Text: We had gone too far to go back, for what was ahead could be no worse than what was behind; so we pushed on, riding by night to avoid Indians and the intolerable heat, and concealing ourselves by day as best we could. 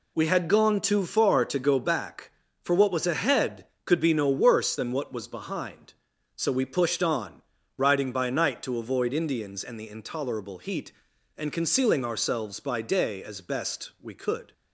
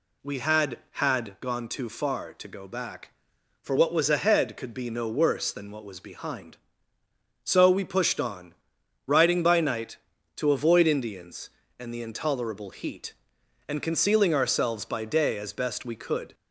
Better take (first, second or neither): first